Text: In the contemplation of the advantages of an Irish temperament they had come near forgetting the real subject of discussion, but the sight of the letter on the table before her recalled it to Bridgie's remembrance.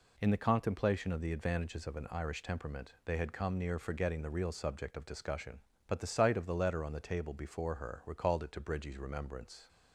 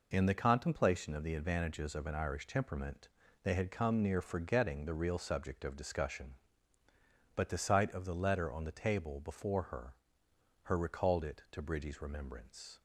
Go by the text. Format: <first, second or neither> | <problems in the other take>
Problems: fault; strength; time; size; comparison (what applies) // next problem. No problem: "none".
first | pauses between "temperament" and "they"; slight; at 3.0 s; 0.36 s long // says "her" twice; at 10.6 s